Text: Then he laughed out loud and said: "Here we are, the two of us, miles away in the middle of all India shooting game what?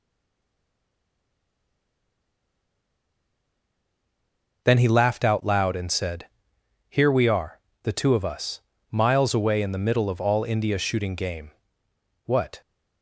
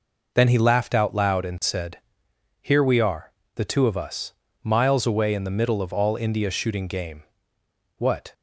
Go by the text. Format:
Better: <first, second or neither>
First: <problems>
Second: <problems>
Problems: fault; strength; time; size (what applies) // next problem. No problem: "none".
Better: second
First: stays silent before the first word; strong; until 4.6 s; 4.6 s long // pauses between "game" and "what"; noticeable; at 11.5 s; 0.76 s long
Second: pauses between "game" and "what"; noticeable; at 7.2 s; 0.76 s long